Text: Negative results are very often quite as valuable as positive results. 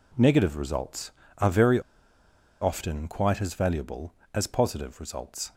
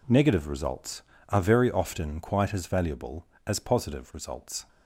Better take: second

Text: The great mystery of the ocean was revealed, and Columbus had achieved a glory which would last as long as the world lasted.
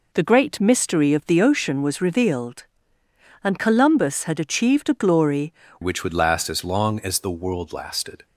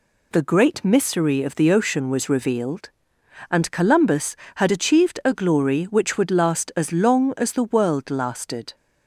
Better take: second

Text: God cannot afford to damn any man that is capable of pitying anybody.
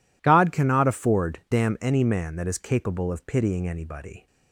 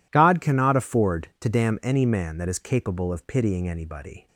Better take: second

